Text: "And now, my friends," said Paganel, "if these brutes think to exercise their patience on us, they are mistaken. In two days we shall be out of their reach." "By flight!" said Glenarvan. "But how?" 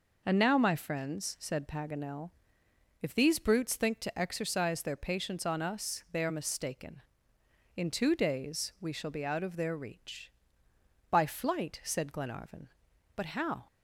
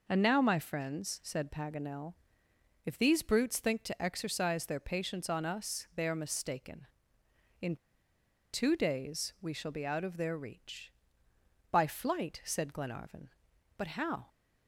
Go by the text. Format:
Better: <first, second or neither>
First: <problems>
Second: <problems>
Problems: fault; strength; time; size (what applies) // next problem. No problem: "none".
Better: first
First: none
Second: pauses between "In" and "two"; noticeable; at 7.7 s; 0.77 s long